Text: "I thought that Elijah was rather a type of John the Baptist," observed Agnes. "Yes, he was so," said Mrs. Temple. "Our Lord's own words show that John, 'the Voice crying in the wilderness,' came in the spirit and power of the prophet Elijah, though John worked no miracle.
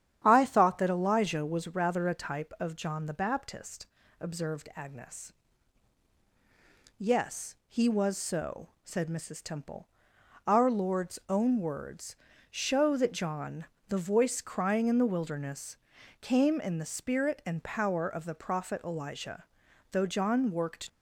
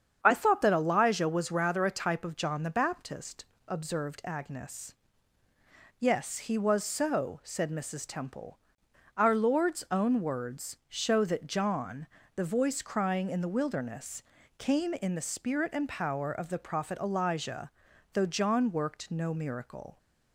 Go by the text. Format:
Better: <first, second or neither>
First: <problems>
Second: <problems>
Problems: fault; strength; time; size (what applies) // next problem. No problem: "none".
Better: second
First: starts louder than the rest; strong; until 1.2 s; 9.5 dB // pauses between "words" and "show"; slight; at 12.1 s; 0.36 s long // stops before "no miracle"; at 20.8 s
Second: starts louder than the rest; strong; until 1.2 s; 7.5 dB